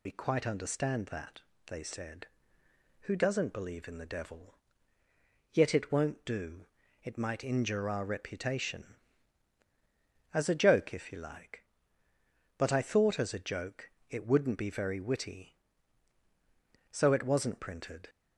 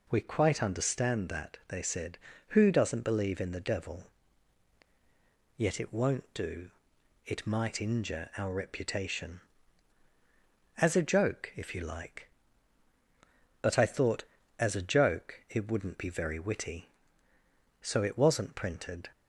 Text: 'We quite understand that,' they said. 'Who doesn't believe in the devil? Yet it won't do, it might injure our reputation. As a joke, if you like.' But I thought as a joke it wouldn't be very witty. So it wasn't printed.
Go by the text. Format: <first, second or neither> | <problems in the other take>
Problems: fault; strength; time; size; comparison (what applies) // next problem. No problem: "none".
second | loses the start of "We"; at 0.0 s; 50 ms // pauses between "joke" and "it"; slight; at 13.9 s; 0.20 s long